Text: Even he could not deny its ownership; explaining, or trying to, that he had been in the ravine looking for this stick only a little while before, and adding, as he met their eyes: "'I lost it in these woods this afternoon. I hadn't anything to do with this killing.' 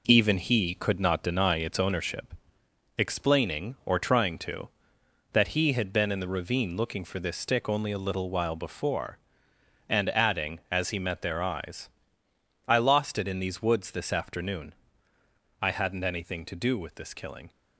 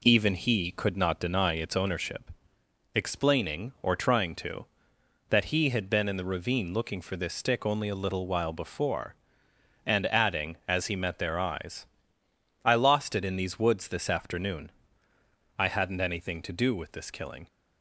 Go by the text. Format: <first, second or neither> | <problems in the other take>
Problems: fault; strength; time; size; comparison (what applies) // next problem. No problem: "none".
second | gets quieter; throughout; 6.5 dB